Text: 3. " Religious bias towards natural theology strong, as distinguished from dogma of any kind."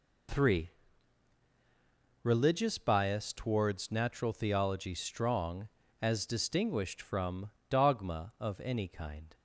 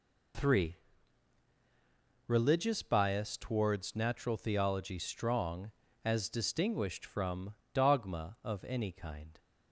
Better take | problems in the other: neither | pauses between "from" and "dogma"; slight; the same in both

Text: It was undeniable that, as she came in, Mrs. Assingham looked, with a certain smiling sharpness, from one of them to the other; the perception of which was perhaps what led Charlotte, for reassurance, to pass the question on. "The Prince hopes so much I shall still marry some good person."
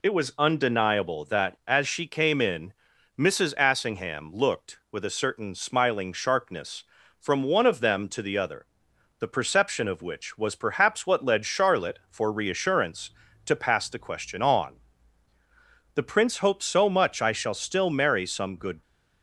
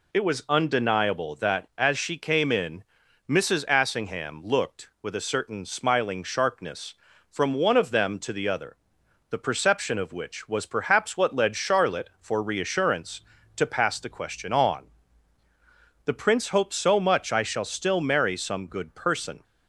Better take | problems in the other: second | stops before "person"; at 18.8 s

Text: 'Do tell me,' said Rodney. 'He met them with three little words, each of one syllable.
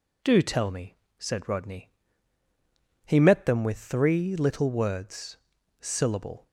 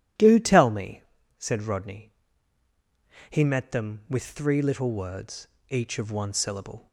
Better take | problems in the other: second | skips "each of one"; at 5.5 s

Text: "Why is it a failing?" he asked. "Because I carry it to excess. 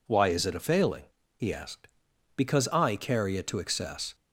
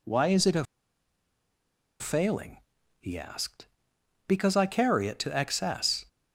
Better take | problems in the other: first | pauses between "a" and "failing"; strong; at 0.6 s; 1.3 s long

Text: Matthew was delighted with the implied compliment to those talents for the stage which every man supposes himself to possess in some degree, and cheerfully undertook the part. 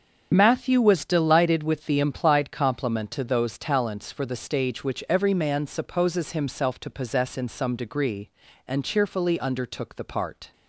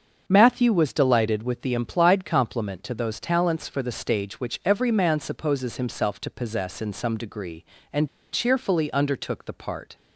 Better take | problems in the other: first | starts louder than the rest; until 1.2 s; 7 dB; strong in the first // pauses between "and" and "cheerfully"; slight; at 8.0 s; 0.24 s long

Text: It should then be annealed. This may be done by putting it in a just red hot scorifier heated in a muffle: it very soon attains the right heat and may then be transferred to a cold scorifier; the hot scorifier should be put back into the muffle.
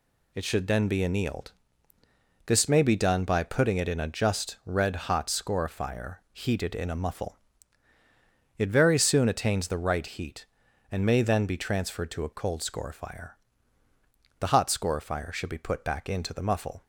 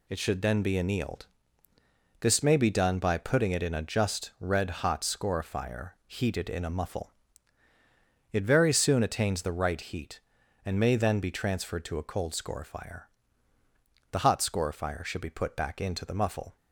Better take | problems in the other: neither | pauses between "scorifier" and "heated"; slight; the same in both

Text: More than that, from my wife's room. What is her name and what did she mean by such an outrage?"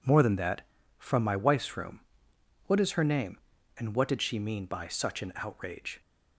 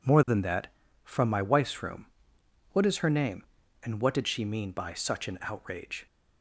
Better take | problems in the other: neither | none

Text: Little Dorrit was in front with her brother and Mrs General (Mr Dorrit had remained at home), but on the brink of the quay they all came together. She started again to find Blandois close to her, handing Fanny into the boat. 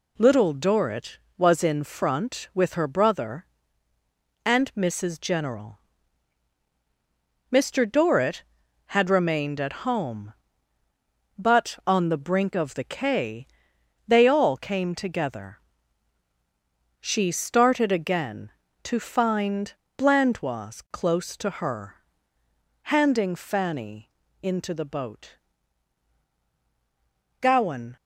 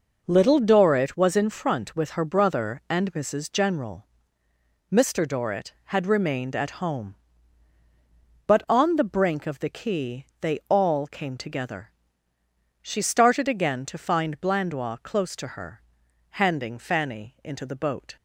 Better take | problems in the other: second | pauses between "quay" and "they"; noticeable; at 13.4 s; 0.58 s long // pauses between "find" and "Blandois"; slight; at 19.7 s; 0.24 s long // pauses between "Fanny" and "into"; slight; at 24.1 s; 0.30 s long // goes on to say "Gowan"; from 27.3 s on; 0.56 s long

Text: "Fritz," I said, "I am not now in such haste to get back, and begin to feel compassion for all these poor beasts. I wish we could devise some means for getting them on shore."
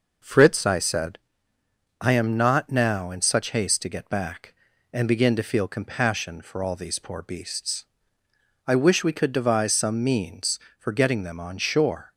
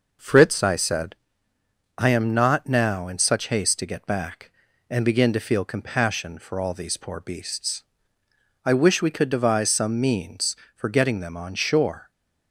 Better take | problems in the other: neither | none

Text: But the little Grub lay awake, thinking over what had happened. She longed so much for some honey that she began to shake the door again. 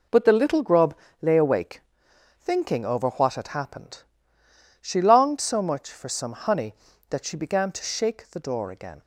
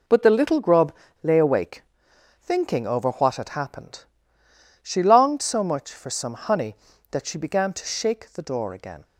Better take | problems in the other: neither | pauses between "Grub" and "lay"; slight; the same in both

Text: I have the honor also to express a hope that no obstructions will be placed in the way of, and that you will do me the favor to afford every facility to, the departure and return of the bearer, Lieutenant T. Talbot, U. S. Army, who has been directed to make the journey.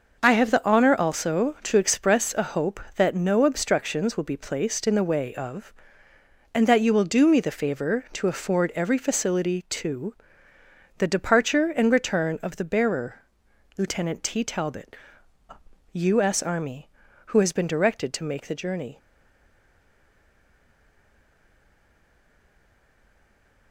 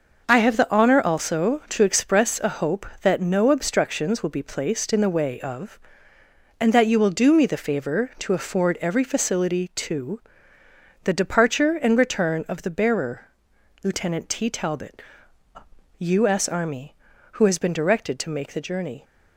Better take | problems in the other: second | stays silent after the last word; strong; from 18.9 s on; 4.8 s long

